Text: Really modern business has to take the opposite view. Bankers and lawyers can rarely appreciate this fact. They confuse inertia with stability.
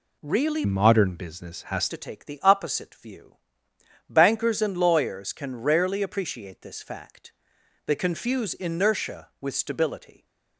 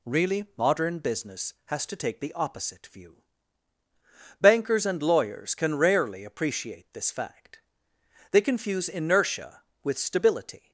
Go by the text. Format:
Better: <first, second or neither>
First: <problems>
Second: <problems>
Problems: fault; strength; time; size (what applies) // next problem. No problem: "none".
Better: second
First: changes voice from "modern" to "has"; from 0.6 to 1.9 s; 1.3 s long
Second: none